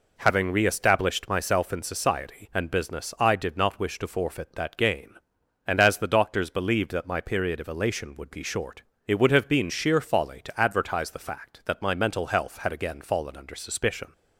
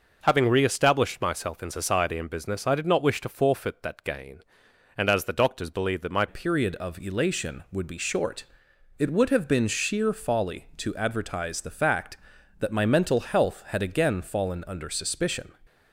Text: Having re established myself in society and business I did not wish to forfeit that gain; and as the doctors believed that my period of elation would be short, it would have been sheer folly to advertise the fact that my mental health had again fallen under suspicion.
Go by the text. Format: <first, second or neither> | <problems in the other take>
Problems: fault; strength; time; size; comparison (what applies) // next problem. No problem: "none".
first | changes voice at "period"; from 6.2 s on; 9.3 s long